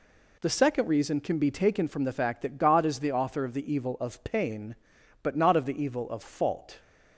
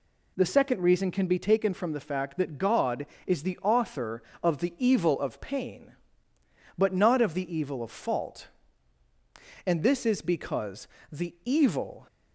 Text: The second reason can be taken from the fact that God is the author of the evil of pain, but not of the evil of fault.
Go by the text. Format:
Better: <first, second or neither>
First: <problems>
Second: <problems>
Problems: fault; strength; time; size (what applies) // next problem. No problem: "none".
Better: first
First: none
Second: goes on to say "And this is because the evil"; strong; from 9.6 s on; 2.4 s long